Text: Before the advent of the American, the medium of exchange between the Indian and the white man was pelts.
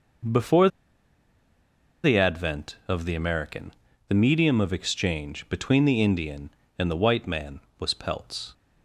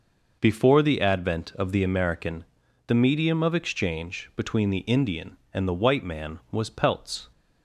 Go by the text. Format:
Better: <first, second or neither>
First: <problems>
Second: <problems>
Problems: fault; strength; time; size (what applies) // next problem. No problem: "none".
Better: second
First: pauses between "Before" and "the"; strong; at 0.6 s; 1.3 s long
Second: none